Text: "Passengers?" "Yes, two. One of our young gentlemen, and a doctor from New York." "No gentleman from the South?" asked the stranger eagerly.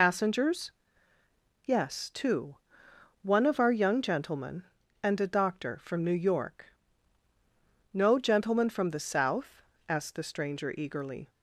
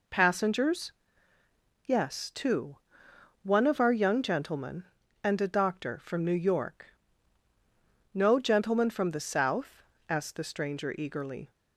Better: second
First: loses the start of "Passengers"; at 0.0 s; 110 ms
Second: none

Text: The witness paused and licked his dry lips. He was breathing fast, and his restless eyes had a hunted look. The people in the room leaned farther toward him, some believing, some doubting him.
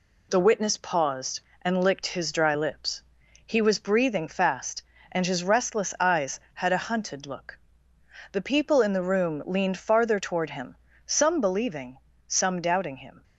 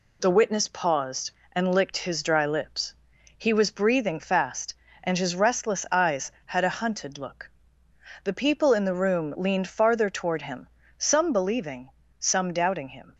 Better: neither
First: none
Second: none

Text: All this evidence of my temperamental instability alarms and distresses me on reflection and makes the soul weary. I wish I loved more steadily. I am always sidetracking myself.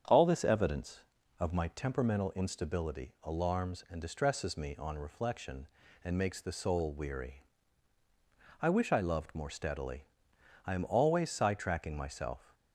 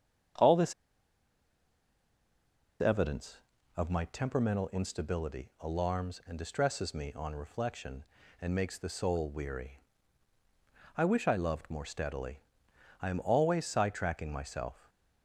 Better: first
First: starts louder than the rest; strong; until 1.4 s; 8 dB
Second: starts louder than the rest; strong; until 3.8 s; 8 dB // pauses between "this" and "evidence"; strong; at 0.7 s; 2.0 s long

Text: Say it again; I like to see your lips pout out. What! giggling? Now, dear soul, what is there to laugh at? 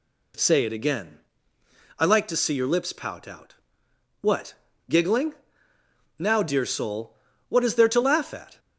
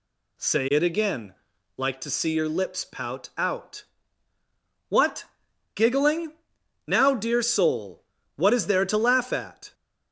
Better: first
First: none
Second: skips "I"; at 1.5 s

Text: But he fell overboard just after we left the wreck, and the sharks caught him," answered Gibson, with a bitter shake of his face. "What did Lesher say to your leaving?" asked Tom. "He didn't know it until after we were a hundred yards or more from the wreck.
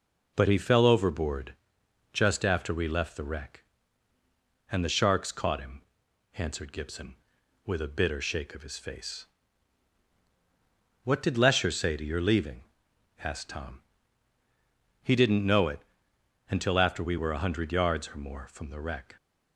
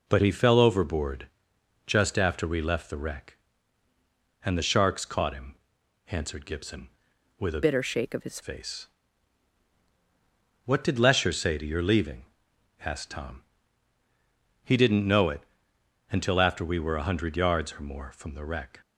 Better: first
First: pauses between "overboard" and "just"; noticeable; at 1.5 s; 0.58 s long // pauses between "it" and "until"; noticeable; at 15.8 s; 0.68 s long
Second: pauses between "overboard" and "just"; noticeable; at 1.2 s; 0.58 s long // changes voice from "bitter" to "his"; from 7.6 to 8.4 s; 0.8 s long // pauses between "it" and "until"; noticeable; at 15.4 s; 0.68 s long

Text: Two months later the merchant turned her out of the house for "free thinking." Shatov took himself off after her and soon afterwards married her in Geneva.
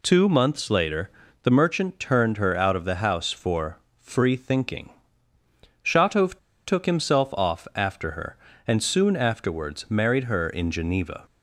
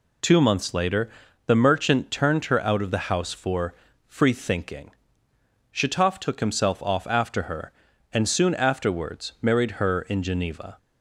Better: second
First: pauses between "later" and "the"; slight; at 1.0 s; 0.34 s long // pauses between "for" and "free"; slight; at 3.7 s; 0.22 s long // pauses between "Shatov" and "took"; slight; at 6.3 s; 0.27 s long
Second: pauses between "later" and "the"; slight; at 1.0 s; 0.36 s long // pauses between "for" and "free"; slight; at 3.7 s; 0.32 s long

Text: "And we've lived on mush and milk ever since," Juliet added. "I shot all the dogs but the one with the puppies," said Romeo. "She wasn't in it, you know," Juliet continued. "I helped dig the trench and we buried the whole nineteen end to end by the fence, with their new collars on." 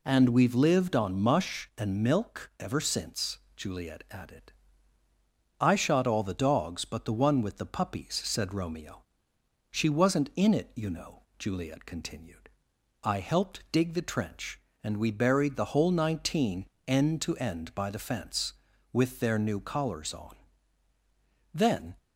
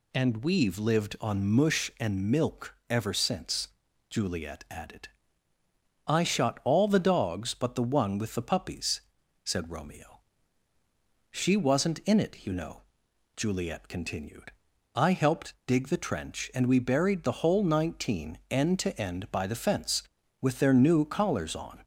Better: second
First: pauses between "nineteen" and "end"; slight; at 16.6 s; 0.22 s long // goes on to say "Then"; slight; from 21.5 s on; 0.40 s long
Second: none

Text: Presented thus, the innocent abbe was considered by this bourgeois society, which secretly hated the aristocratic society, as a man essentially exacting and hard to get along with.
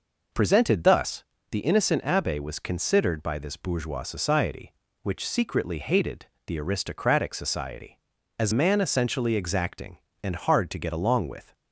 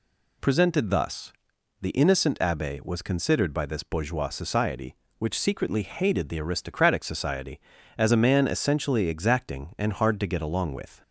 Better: second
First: pauses between "hated" and "the"; slight; at 6.2 s; 0.20 s long // skips "a"; at 8.5 s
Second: none

